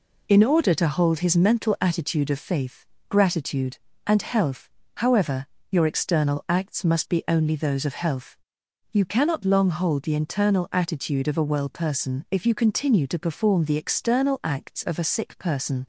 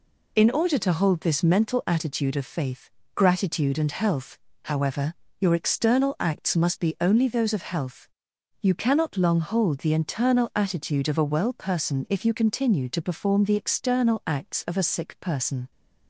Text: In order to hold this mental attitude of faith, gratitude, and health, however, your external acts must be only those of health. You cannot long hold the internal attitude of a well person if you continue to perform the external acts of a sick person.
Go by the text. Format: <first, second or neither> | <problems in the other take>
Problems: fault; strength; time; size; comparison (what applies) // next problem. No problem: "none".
second | says "his" for "this"; at 1.1 s